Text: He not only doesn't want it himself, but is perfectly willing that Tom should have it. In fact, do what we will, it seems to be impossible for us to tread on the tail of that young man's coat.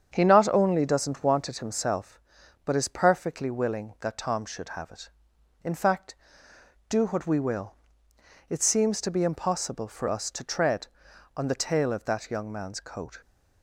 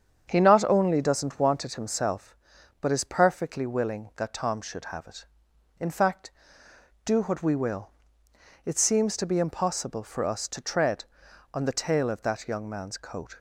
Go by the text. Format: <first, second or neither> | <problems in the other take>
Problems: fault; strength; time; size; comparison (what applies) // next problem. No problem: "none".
neither | starts louder than the rest; strong; the same in both